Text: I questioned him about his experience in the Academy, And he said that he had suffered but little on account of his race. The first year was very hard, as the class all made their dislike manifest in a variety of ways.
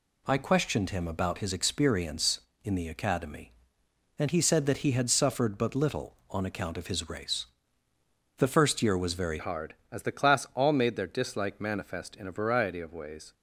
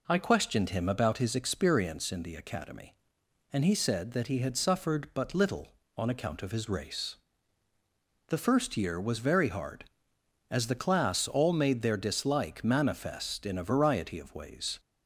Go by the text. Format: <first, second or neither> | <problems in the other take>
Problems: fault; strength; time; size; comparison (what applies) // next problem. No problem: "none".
second | changes voice at "hard"; from 9.3 s on; 4.0 s long